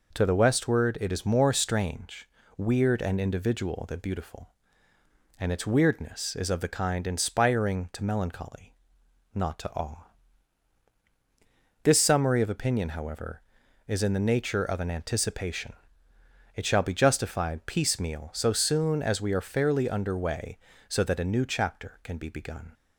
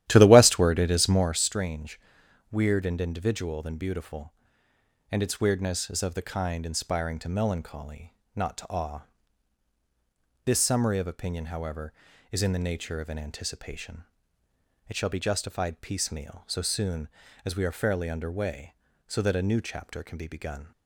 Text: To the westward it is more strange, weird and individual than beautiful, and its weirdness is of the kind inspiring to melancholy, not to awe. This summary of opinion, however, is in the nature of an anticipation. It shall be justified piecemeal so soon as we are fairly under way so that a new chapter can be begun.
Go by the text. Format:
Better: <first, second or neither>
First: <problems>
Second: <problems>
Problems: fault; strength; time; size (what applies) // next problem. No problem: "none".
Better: first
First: none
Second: starts louder than the rest; strong; until 1.4 s; 12.5 dB